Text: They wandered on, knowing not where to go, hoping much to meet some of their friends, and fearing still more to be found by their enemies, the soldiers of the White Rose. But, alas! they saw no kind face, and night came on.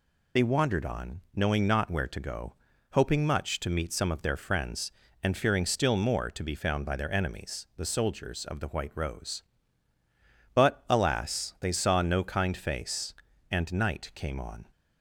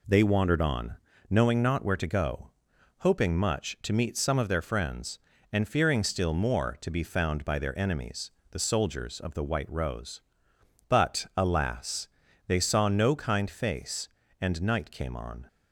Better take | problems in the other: second | loses the start of "They"; at 0.3 s; 35 ms

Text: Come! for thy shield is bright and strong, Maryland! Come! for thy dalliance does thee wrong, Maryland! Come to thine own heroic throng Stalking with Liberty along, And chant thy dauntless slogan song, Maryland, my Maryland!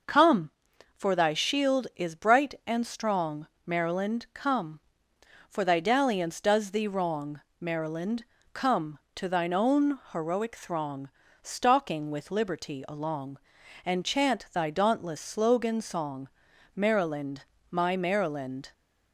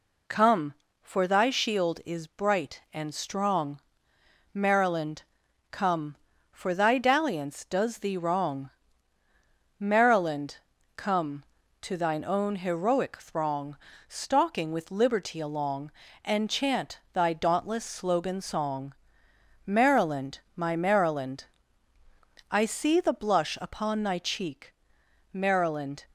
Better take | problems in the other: first | pauses between "throng" and "Stalking"; slight; at 13.7 s; 0.32 s long; slight in the first // goes on to say "I see the blush upon thy cheek Maryland"; strong; from 22.4 s on; 3.5 s long

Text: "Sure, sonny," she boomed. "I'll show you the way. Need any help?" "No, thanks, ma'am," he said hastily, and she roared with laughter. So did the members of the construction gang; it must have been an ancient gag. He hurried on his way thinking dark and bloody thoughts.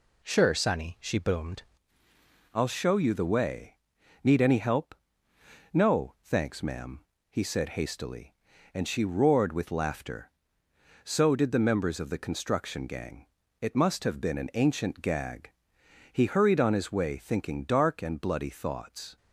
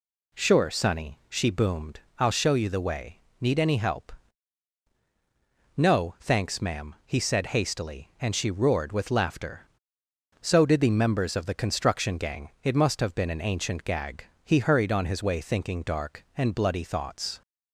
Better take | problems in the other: second | changes voice at "I'll"; from 2.5 s on; 16.6 s long

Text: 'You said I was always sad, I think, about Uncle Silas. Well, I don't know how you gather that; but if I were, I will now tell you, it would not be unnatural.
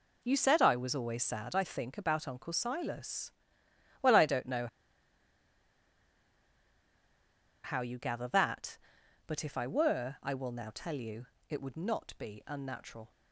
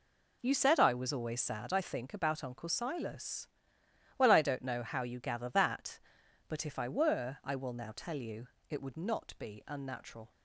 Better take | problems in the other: second | pauses between "know" and "how"; strong; at 4.6 s; 2.9 s long

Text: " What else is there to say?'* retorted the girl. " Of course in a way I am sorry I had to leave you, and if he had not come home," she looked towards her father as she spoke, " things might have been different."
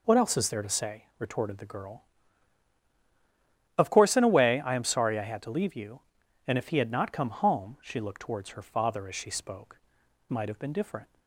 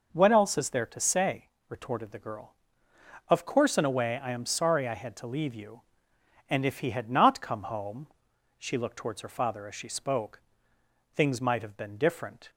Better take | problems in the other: second | skips "things"; at 10.2 s

